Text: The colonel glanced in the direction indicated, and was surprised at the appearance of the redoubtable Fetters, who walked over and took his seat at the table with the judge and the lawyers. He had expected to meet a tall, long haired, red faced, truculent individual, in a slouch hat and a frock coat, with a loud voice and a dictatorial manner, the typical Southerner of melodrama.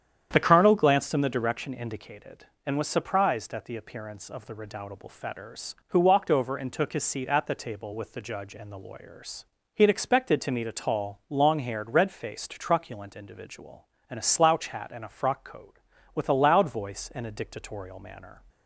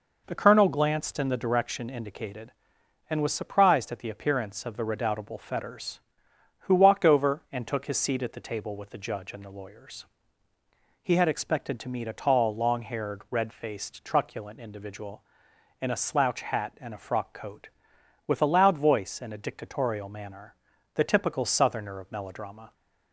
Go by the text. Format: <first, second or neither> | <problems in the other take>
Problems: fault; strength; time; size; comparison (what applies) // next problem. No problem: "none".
second | starts louder than the rest; strong; until 1.3 s; 9 dB // stops before "the typical Southerner of melodrama"; at 18.4 s